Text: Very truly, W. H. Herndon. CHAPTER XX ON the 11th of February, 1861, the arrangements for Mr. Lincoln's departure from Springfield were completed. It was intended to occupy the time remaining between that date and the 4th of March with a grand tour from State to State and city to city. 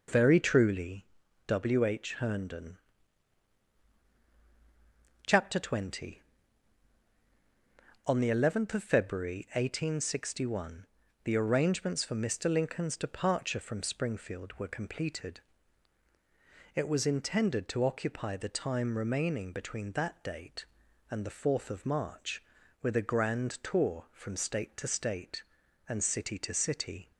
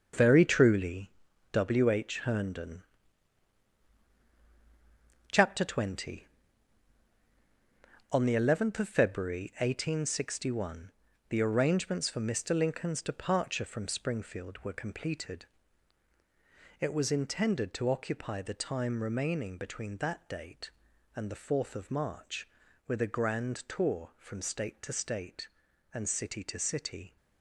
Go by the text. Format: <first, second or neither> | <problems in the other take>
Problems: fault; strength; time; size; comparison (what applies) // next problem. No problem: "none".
first | gets quieter; strong; throughout; 9 dB